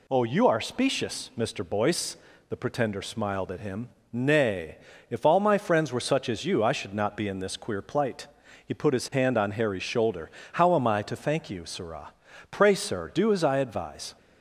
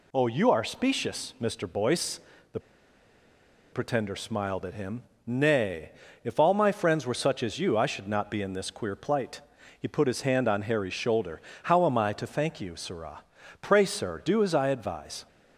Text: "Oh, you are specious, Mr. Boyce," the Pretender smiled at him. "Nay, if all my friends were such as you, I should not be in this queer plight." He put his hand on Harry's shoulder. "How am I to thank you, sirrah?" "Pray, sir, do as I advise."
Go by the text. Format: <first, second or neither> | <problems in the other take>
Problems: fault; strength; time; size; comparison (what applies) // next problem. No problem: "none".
first | pauses between "the" and "Pretender"; at 2.6 s; 1.1 s long